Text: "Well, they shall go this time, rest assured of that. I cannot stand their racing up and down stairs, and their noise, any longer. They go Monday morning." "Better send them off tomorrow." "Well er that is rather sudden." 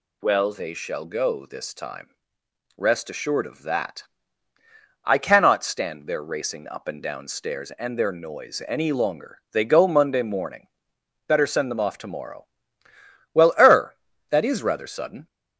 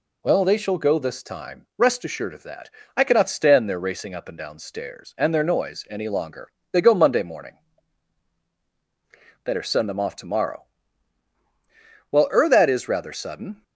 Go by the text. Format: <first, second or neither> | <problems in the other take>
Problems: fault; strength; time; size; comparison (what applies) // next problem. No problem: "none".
neither | none